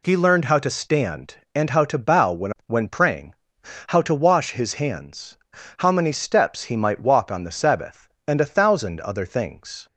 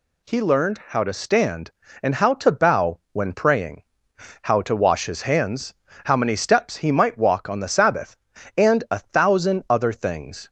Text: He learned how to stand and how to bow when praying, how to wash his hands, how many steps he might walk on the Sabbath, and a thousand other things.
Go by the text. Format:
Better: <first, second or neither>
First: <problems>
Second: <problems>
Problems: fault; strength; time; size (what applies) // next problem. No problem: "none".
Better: second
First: says "when" twice; at 2.6 s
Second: none